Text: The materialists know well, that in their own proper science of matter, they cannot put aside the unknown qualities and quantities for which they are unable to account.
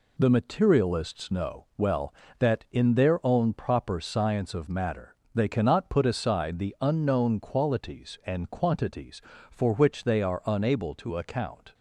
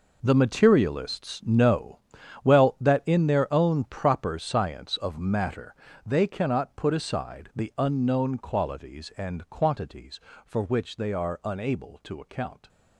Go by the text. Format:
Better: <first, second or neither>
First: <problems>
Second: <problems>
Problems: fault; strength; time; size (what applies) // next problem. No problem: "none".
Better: first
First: none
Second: gets quieter; strong; throughout; 14 dB // pauses between "know" and "well"; noticeable; at 1.9 s; 0.46 s long